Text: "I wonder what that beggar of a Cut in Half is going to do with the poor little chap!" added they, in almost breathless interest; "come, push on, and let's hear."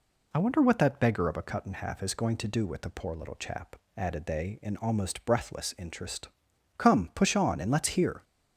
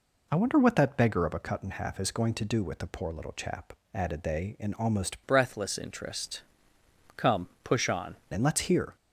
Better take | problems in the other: first | changes voice from "breathless" to "on"; from 5.2 to 8.1 s; 2.9 s long

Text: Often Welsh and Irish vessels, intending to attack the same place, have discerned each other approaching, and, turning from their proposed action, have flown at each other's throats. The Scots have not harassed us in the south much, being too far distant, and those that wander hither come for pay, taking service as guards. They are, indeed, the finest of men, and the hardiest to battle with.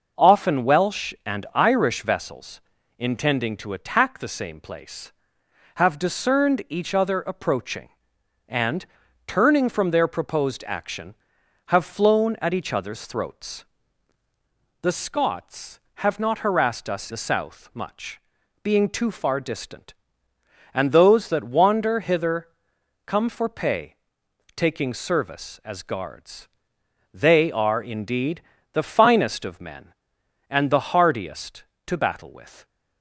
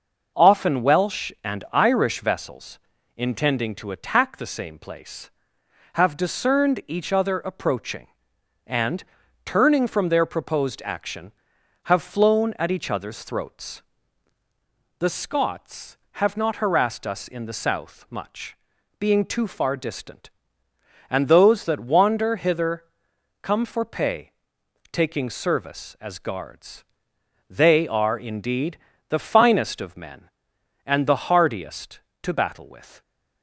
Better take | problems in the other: second | skips "in"; at 17.1 s // pauses between "hither" and "come"; noticeable; at 22.4 s; 0.56 s long; noticeable in the second

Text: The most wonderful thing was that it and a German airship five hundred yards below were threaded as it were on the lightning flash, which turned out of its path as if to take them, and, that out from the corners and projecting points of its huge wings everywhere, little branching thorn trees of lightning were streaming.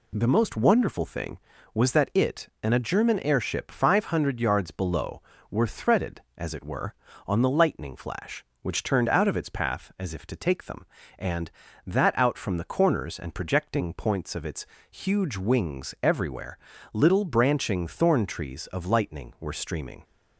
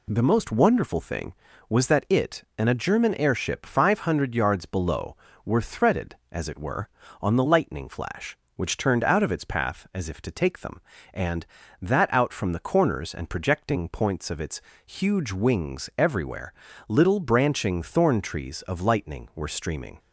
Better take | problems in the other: neither | pauses between "its" and "huge"; slight; the same in both

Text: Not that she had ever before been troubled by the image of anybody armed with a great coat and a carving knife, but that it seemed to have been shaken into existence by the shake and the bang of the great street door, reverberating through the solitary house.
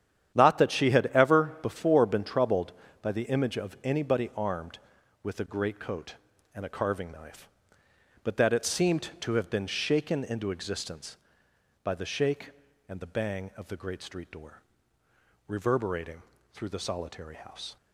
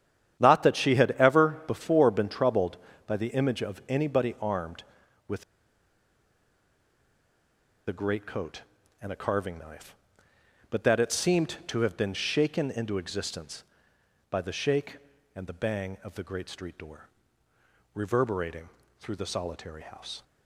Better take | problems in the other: first | starts louder than the rest; strong; until 1.4 s; 10 dB; strong in the first // pauses between "with" and "a"; strong; at 5.4 s; 2.4 s long // pauses between "reverberating" and "through"; slight; at 18.6 s; 0.30 s long; slight in the first

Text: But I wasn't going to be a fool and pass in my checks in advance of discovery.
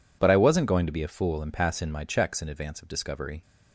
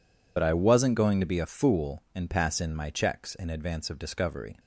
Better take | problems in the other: first | loses the start of "But"; at 0.3 s; 50 ms

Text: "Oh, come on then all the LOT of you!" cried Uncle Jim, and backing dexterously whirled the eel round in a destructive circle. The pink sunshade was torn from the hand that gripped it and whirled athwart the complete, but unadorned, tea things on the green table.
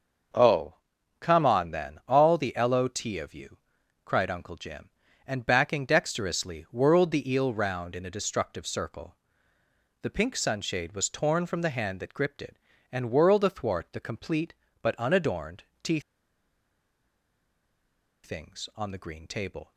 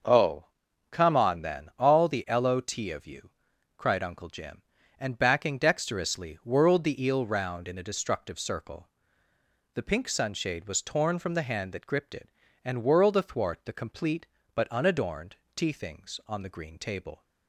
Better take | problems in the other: second | starts louder than the rest; until 1.7 s; 6 dB; also in the second // pauses between "tea" and "things"; strong; at 15.9 s; 2.2 s long

